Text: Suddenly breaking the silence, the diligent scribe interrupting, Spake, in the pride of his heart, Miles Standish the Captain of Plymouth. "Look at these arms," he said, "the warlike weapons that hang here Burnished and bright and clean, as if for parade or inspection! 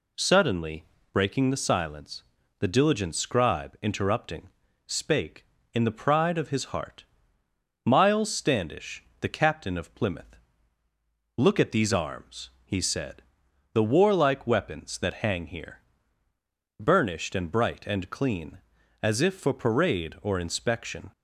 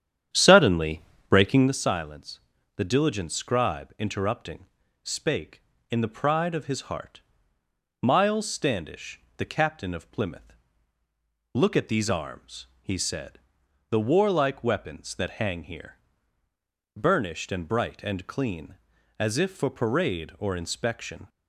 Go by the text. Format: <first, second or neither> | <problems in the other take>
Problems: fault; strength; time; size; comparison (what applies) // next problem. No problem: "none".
first | starts louder than the rest; strong; until 1.8 s; 9.5 dB // pauses between "Suddenly" and "breaking"; slight; at 1.0 s; 0.26 s long; slight in the first // pauses between "Standish" and "the"; slight; at 9.2 s; 0.16 s long; slight in the first // pauses between "here" and "Burnished"; noticeable; at 15.9 s; 0.98 s long; noticeable in the first